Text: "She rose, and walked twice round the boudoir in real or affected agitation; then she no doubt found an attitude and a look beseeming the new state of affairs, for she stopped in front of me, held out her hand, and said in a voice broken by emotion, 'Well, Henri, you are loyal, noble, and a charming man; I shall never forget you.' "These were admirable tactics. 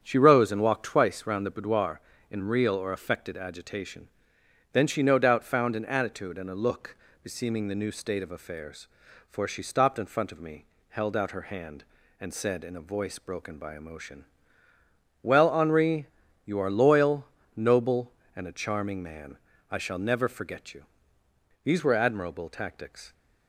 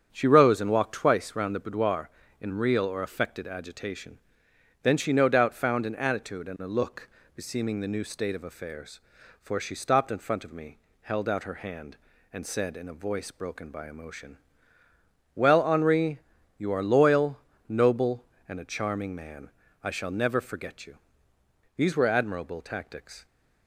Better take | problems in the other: neither | starts louder than the rest; strong; the same in both // pauses between "look" and "beseeming"; slight; the same in both

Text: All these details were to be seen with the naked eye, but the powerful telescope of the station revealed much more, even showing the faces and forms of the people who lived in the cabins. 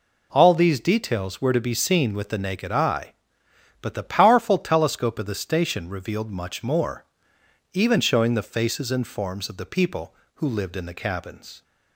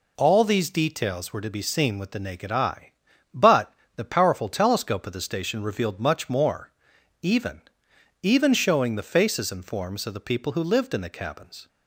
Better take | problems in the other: first | pauses between "but" and "the"; slight; at 3.7 s; 0.24 s long // says "even" twice; at 8.2 s

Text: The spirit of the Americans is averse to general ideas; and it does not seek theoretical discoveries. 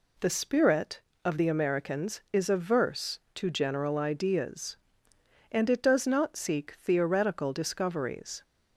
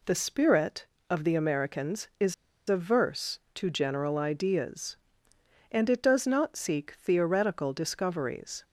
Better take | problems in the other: first | pauses between "is" and "averse"; slight; at 2.3 s; 0.33 s long

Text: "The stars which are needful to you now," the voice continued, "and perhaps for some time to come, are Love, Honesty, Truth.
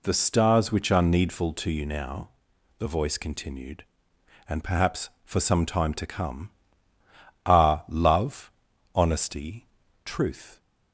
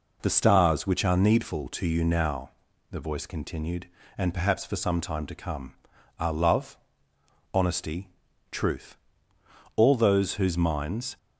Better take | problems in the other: first | goes on to say "All those whose minds"; from 9.7 s on; 1.4 s long

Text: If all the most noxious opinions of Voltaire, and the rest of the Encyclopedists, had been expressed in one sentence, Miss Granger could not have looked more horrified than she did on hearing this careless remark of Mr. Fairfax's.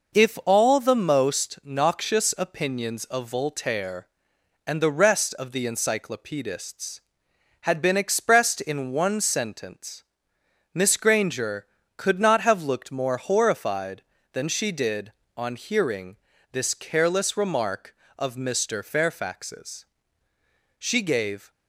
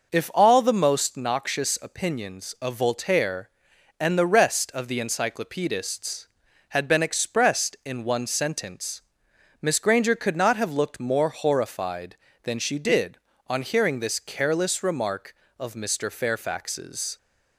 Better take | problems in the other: second | pauses between "hearing" and "this"; slight; at 16.1 s; 0.36 s long // goes on to say "She gave"; noticeable; from 20.7 s on; 0.72 s long

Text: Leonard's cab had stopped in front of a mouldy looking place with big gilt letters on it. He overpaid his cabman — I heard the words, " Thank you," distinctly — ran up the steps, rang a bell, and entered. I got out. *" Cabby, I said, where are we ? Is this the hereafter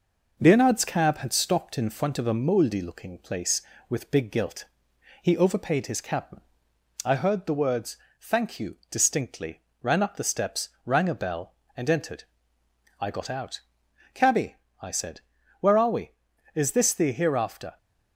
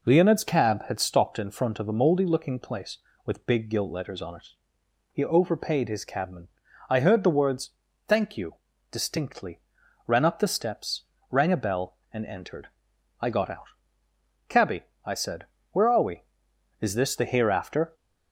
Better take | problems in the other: second | skips "letters on it"; at 4.9 s

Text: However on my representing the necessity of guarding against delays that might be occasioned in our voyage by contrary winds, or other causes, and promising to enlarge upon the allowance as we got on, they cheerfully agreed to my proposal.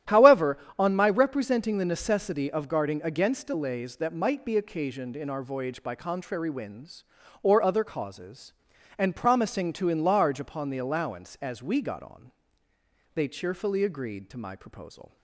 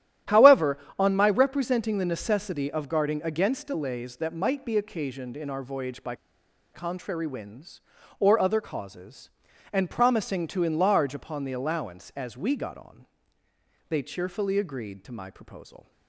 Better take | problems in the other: first | starts louder than the rest; strong; until 1.4 s; 11.5 dB; strong in the first // pauses between "by" and "contrary"; noticeable; at 6.1 s; 0.59 s long

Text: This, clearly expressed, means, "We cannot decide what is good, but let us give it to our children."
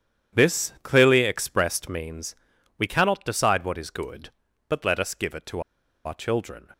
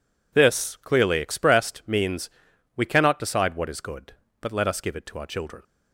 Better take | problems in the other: second | pauses between "to" and "our"; at 5.5 s; 0.45 s long

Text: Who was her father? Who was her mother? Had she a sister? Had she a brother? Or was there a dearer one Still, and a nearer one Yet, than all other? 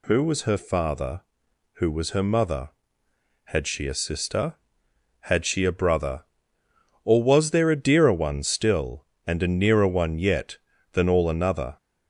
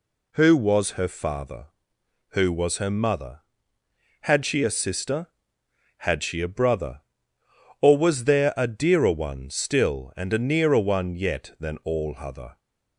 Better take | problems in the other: second | says "another" for "other"; at 11.3 s

